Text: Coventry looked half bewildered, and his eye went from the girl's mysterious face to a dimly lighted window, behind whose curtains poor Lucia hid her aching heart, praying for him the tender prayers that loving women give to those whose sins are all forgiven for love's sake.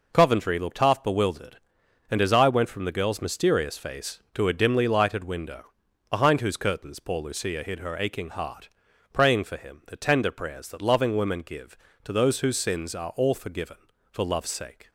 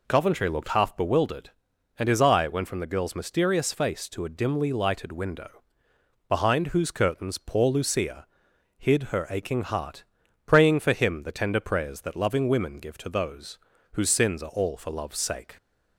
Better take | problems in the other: first | pauses between "Lucia" and "hid"; noticeable; at 8.2 s; 0.50 s long // pauses between "those" and "whose"; slight; at 13.5 s; 0.36 s long // skips "forgiven"; at 14.7 s

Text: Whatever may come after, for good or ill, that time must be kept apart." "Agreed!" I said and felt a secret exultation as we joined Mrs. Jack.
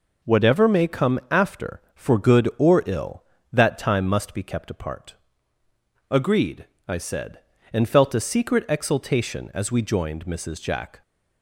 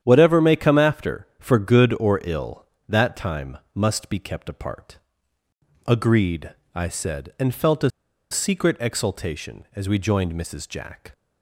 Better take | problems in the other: first | starts louder than the rest; strong; until 1.0 s; 9.5 dB // pauses between "time" and "must"; slight; at 3.5 s; 0.16 s long // pauses between "a" and "secret"; at 7.8 s; 0.41 s long

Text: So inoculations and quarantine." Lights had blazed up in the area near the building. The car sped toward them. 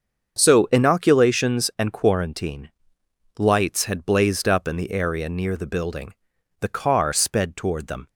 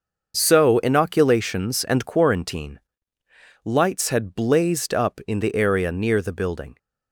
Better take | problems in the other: first | starts louder than the rest; until 1.3 s; 6.5 dB; also in the first // stops before "The car sped toward them"; at 6.7 s

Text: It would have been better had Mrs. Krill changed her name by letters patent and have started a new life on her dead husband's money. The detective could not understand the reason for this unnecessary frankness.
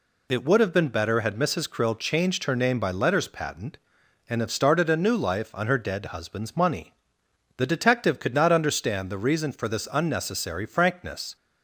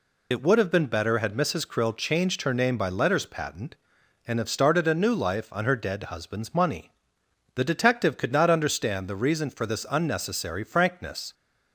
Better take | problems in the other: first | loses the start of "It"; at 0.3 s; 35 ms

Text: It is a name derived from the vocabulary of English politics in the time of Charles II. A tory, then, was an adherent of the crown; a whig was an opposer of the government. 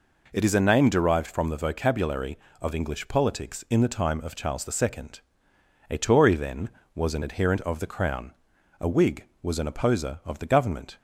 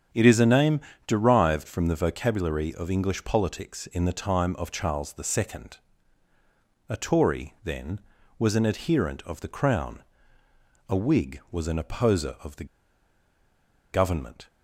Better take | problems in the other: first | starts louder than the rest; strong; until 1.4 s; 8 dB // pauses between "name" and "derived"; slight; at 0.8 s; 0.26 s long // pauses between "the" and "government"; strong; at 12.6 s; 1.2 s long

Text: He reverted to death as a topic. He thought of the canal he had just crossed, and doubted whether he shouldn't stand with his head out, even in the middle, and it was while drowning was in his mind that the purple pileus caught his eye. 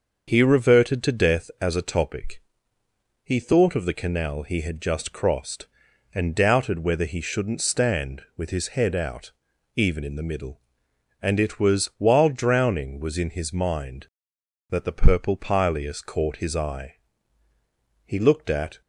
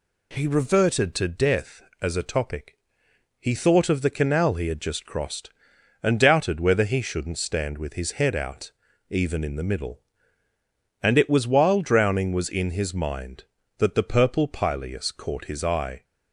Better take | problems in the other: second | starts louder than the rest; until 1.3 s; 6.5 dB // goes on to say "He looked at"; noticeable; from 18.0 s on; 0.76 s long

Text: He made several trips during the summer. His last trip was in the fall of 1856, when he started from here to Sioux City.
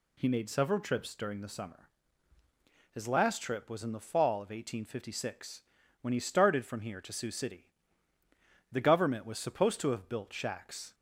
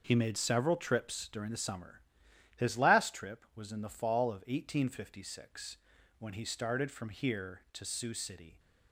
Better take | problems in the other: second | goes on to say "The government was supposed to have built shacks"; strong; from 8.7 s on; 2.2 s long

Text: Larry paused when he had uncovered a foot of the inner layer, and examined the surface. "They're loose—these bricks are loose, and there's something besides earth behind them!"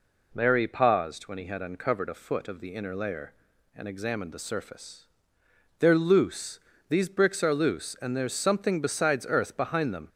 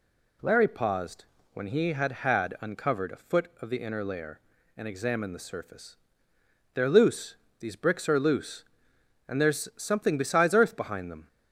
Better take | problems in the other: first | pauses between "paused" and "when"; slight; at 1.2 s; 0.28 s long // says "had" twice; at 2.1 s

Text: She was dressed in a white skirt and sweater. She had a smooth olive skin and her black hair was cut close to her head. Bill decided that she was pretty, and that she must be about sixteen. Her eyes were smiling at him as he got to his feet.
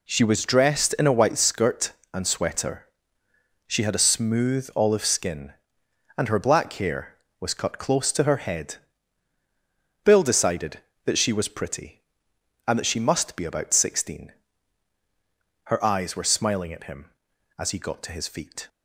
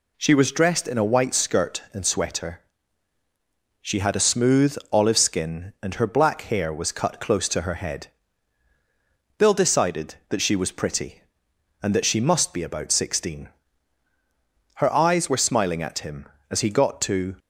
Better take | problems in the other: first | stops before "his feet"; at 17.3 s

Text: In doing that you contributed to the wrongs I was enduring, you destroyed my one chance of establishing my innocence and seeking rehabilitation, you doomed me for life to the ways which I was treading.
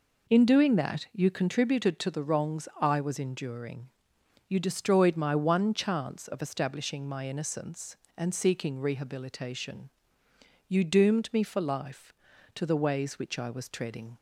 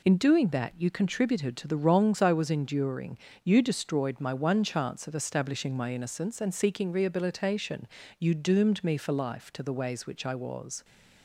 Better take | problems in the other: first | stops before "treading"; at 10.8 s

